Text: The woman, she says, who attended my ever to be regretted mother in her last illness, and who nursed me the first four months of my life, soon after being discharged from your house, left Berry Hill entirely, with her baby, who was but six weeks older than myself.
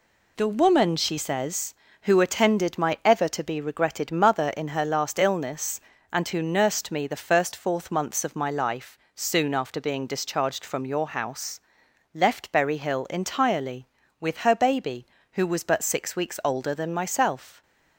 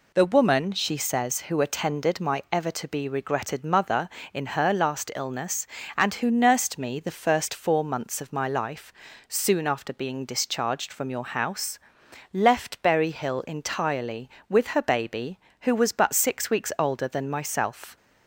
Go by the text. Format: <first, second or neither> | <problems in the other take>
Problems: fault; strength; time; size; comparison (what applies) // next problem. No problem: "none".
second | says "fourth" for "four"; at 7.5 s